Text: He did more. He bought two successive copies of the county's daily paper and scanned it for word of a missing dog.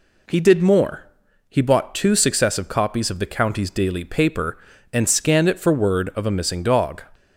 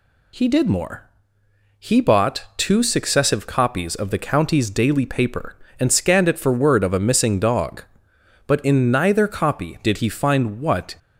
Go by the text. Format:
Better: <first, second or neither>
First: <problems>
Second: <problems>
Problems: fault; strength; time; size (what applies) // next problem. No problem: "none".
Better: first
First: none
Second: goes on to say "But in neither copy did he find what"; strong; from 8.4 s on; 2.4 s long